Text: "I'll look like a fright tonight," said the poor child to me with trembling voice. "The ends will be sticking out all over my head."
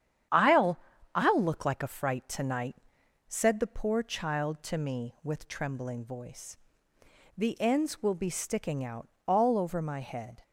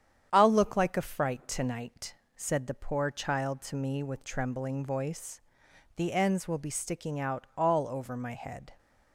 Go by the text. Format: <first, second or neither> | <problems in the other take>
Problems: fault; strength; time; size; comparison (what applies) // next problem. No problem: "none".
second | starts louder than the rest; strong; until 1.6 s; 9.5 dB; strong in the second // says "I'll" twice; at 1.1 s // pauses between "out" and "all"; slight; at 9.0 s; 0.16 s long